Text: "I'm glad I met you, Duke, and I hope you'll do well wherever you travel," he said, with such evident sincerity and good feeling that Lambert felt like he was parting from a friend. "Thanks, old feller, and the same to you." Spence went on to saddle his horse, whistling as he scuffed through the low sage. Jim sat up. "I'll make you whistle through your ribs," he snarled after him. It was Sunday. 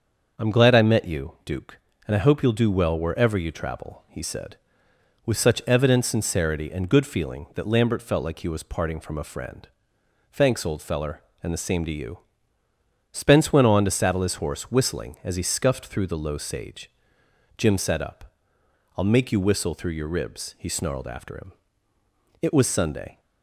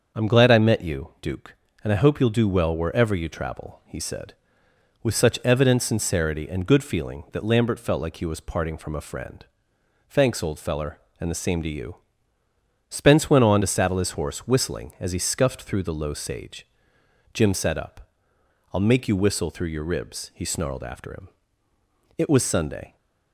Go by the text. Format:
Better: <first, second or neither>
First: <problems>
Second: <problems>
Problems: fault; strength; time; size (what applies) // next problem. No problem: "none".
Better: neither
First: starts louder than the rest; until 1.4 s; 6.5 dB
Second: starts louder than the rest; until 1.2 s; 6.5 dB